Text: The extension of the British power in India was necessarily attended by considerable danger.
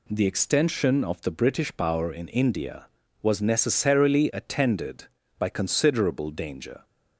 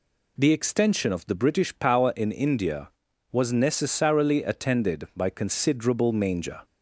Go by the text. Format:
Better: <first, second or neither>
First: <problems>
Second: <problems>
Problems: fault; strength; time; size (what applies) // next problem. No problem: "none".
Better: first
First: none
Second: says "manger" for "danger"; at 6.1 s